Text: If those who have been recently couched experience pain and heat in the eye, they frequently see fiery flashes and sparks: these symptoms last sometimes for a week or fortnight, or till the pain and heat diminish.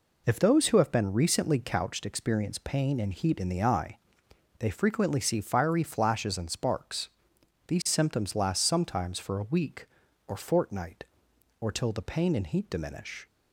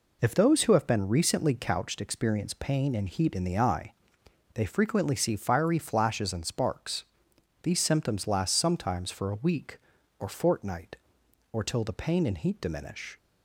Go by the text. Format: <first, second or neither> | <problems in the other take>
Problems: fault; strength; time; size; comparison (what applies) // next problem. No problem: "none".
neither | none